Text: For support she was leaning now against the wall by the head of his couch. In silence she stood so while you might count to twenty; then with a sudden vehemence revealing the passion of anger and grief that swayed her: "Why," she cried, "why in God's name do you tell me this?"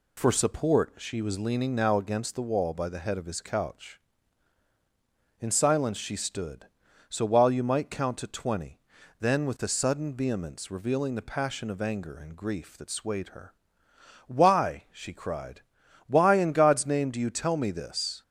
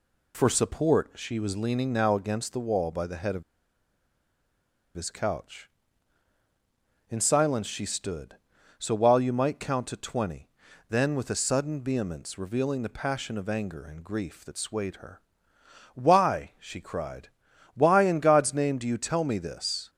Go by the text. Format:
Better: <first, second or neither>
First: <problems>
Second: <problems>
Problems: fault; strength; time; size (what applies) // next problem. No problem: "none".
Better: first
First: none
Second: pauses between "of" and "his"; strong; at 3.4 s; 1.5 s long